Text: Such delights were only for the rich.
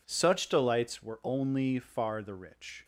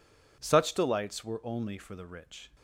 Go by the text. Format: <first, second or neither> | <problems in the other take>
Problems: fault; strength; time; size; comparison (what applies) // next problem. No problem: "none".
second | says "far" for "for"; at 1.7 s